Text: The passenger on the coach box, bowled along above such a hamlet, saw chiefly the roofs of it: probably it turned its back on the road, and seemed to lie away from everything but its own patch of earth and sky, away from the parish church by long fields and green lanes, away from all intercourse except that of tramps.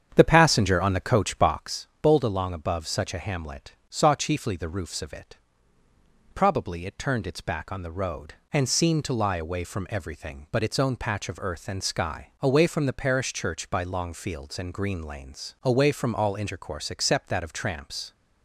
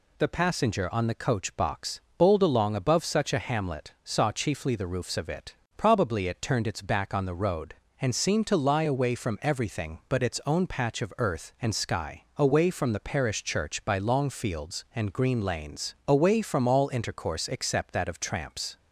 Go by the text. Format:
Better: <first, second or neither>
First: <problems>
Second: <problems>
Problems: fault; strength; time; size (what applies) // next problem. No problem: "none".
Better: second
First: starts louder than the rest; strong; until 1.6 s; 8 dB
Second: none